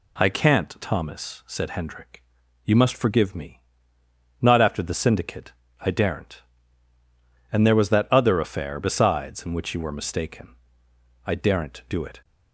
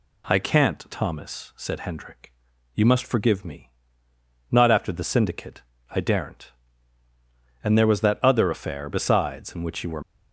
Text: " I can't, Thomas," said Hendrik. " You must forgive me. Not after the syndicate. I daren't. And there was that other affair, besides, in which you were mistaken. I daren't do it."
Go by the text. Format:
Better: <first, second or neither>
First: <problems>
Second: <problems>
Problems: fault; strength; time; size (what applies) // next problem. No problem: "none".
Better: first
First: none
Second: stops before "mistaken I daren't do it"; at 10.0 s